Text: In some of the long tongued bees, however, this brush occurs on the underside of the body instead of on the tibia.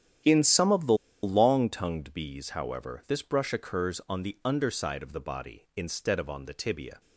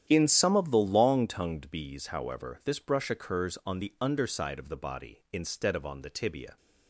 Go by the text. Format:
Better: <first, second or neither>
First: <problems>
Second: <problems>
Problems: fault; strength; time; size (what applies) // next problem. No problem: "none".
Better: second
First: starts louder than the rest; strong; until 1.5 s; 10 dB // pauses between "the" and "long"; slight; at 0.9 s; 0.29 s long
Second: starts louder than the rest; strong; until 1.0 s; 10 dB